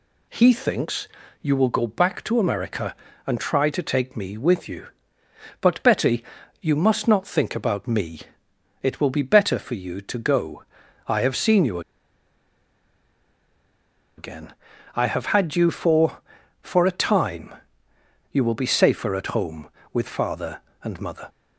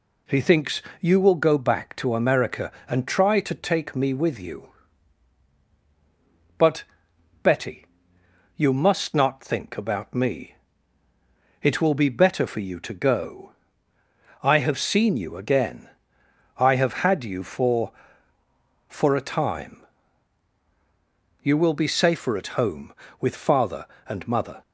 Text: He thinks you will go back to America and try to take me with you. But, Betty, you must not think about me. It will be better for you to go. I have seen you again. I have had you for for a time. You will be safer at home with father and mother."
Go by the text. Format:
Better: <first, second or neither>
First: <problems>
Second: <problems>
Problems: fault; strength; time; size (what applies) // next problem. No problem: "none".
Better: second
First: pauses between "thinks" and "you"; slight; at 1.0 s; 0.34 s long // pauses between "you" and "again"; strong; at 11.7 s; 2.3 s long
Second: pauses between "thinks" and "you"; slight; at 0.8 s; 0.18 s long